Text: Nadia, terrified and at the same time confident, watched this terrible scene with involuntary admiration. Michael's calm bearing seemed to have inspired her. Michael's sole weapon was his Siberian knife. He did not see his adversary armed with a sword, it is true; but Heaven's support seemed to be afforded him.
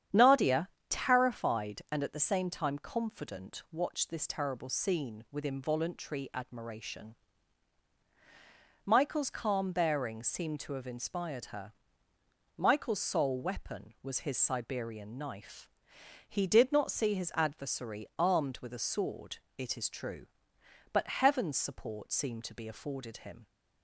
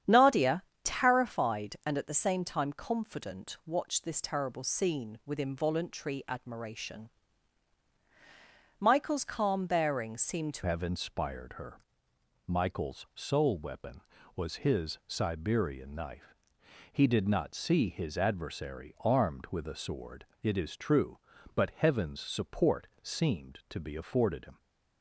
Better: first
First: starts louder than the rest; strong; until 1.3 s; 9 dB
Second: starts louder than the rest; strong; until 1.2 s; 9 dB // changes voice at "have"; from 10.6 s on; 13.9 s long

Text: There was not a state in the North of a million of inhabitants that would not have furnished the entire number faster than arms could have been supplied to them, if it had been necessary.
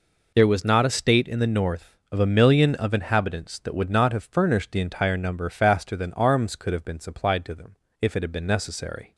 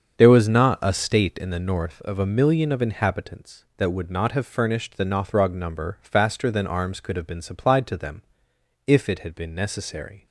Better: first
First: none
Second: starts louder than the rest; until 1.1 s; 7 dB // says "nothrog" for "entire"; at 5.0 s

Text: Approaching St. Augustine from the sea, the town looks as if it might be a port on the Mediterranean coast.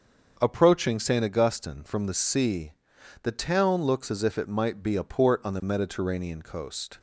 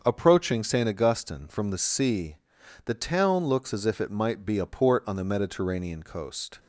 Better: neither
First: starts louder than the rest; until 1.4 s; 6.5 dB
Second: starts louder than the rest; until 1.0 s; 6.5 dB

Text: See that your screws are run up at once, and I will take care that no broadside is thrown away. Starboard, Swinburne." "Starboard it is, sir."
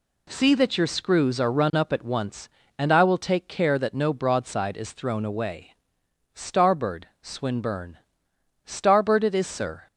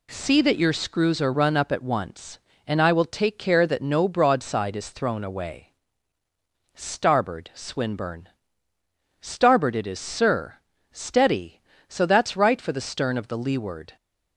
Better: first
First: none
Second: goes on to say "Steady so that's right for the stern of the leeward"; strong; from 10.9 s on; 3.0 s long

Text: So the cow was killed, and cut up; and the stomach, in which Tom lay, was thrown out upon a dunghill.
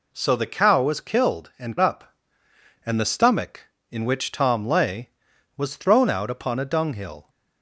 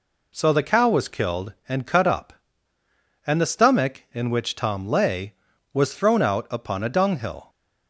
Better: second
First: skips "cut"; at 1.7 s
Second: none

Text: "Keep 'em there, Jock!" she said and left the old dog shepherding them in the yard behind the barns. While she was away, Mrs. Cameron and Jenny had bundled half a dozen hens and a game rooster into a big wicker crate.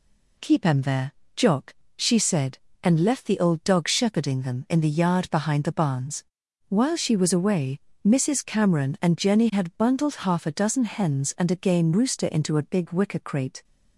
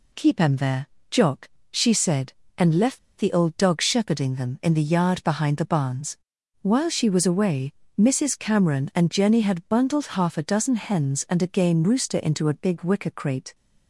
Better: first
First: none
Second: pauses between "left" and "the"; slight; at 2.9 s; 0.19 s long

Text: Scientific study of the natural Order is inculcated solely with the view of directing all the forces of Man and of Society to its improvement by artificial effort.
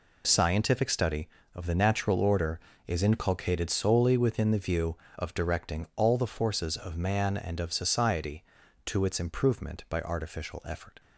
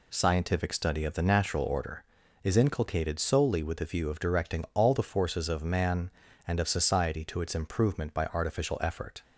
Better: second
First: says "within" for "with"; at 4.1 s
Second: none

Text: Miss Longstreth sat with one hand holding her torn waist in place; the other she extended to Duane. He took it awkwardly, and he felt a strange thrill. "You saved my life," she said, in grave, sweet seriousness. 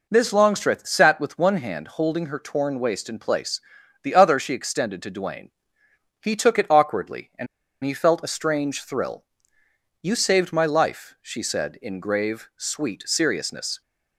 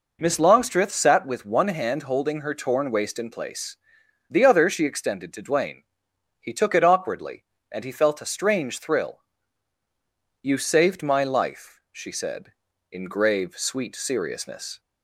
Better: second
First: pauses between "and" and "he"; at 7.4 s; 0.38 s long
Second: none

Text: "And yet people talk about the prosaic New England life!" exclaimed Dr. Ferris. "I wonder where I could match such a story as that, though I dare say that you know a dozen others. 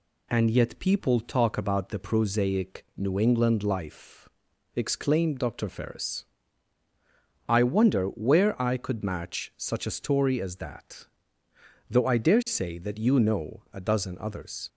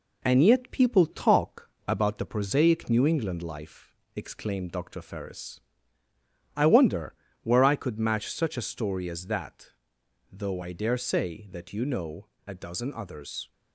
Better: first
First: none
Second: gets quieter; slight; throughout; 2.5 dB // pauses between "talk" and "about"; slight; at 1.7 s; 0.16 s long // pauses between "wonder" and "where"; slight; at 7.1 s; 0.30 s long // pauses between "know" and "a"; slight; at 12.2 s; 0.18 s long

